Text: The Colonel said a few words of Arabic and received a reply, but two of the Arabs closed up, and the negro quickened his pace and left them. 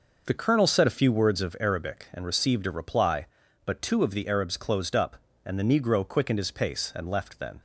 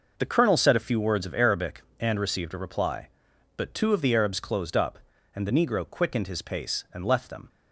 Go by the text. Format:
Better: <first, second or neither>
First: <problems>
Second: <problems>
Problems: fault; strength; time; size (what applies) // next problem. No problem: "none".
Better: second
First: says "then" for "them"; at 7.3 s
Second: none